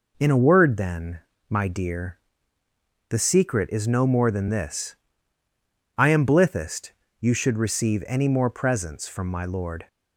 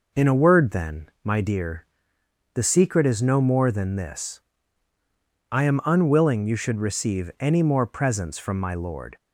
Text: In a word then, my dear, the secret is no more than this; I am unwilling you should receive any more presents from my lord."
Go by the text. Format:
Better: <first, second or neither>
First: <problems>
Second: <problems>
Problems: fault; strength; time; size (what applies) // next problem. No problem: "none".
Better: second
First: says "blithest" for "unwilling"; at 6.2 s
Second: none